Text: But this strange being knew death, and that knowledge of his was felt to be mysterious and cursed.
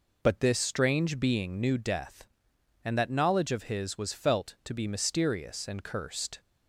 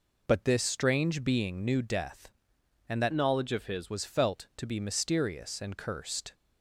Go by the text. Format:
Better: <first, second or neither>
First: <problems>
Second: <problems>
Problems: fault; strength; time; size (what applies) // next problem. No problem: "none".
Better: first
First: none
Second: changes voice from "knowledge" to "his"; from 3.1 to 3.9 s; 0.8 s long